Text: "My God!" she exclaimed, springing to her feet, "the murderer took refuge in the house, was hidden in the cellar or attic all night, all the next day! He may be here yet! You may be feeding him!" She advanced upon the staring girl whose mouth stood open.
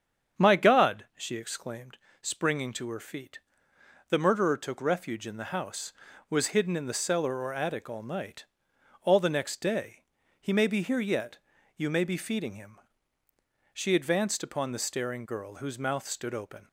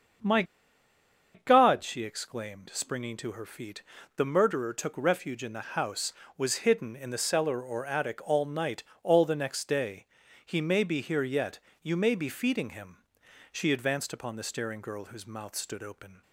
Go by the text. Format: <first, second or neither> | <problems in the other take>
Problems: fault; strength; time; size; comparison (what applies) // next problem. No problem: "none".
first | starts louder than the rest; until 2.1 s; 7 dB; strong in the first // pauses between "My" and "God"; noticeable; at 0.4 s; 0.91 s long